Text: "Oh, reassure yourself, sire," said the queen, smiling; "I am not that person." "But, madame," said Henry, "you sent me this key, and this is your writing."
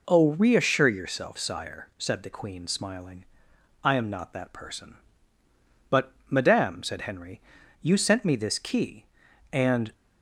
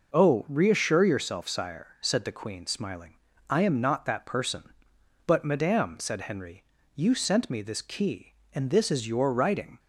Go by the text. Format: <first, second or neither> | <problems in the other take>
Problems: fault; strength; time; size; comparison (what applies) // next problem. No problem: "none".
second | stops before "this is your writing"; at 9.9 s